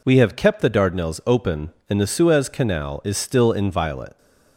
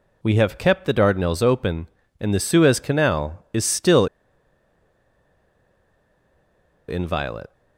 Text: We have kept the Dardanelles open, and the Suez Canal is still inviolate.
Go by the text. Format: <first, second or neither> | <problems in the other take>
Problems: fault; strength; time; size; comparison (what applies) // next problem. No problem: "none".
first | pauses between "still" and "inviolate"; strong; at 4.0 s; 2.8 s long